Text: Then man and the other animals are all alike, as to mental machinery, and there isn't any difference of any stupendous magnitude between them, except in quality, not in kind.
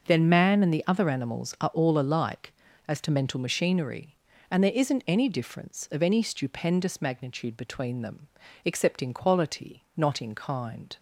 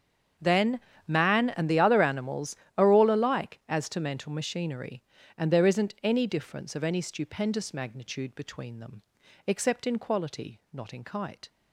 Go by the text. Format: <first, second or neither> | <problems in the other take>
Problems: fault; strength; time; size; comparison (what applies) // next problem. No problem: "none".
first | starts louder than the rest; strong; until 1.6 s; 7.5 dB // pauses between "Then" and "man"; slight; at 0.7 s; 0.28 s long // says "kite" for "kind"; at 11.0 s